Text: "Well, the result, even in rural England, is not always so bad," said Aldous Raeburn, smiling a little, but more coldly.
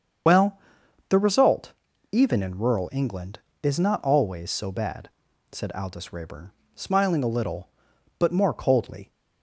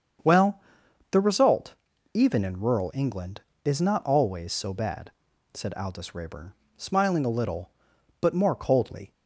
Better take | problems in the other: second | loses the start of "Well"; at 0.2 s; 80 ms // starts louder than the rest; strong; until 2.1 s; 7 dB; strong in the second

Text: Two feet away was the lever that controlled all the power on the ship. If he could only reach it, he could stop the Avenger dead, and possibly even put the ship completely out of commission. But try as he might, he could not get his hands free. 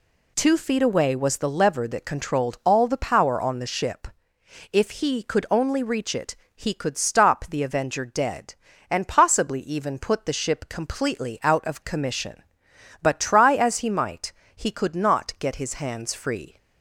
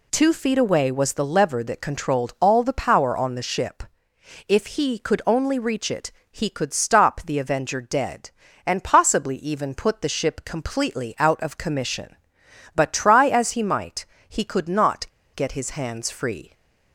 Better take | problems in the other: first | pauses between "not" and "get"; slight; at 15.0 s; 0.29 s long

